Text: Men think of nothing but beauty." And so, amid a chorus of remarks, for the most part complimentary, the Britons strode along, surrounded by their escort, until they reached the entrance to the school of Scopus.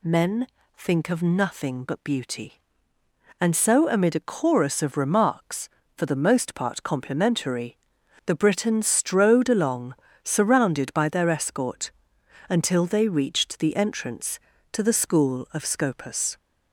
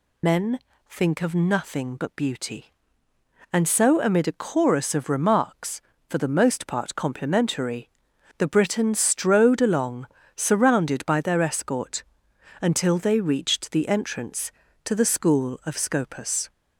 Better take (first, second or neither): first